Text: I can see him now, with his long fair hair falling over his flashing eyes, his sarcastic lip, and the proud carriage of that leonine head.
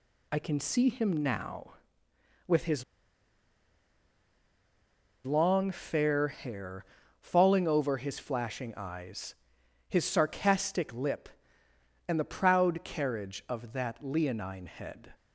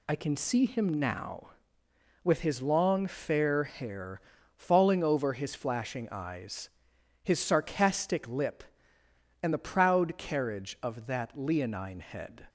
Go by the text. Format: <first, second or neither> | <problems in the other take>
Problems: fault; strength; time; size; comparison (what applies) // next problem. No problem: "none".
second | pauses between "his" and "long"; strong; at 2.8 s; 2.4 s long // pauses between "hair" and "falling"; slight; at 6.8 s; 0.34 s long; slight in the second